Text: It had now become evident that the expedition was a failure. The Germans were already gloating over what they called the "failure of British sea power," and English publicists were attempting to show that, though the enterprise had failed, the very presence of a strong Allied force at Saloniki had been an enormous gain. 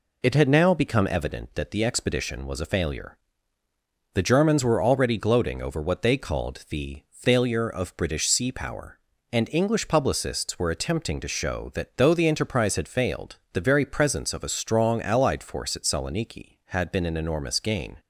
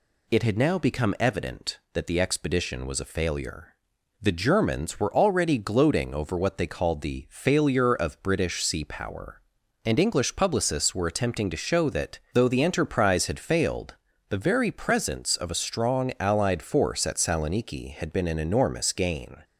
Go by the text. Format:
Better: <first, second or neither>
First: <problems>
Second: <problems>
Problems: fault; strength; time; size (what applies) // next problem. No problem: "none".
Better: second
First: starts louder than the rest; slight; until 1.3 s; 3 dB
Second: none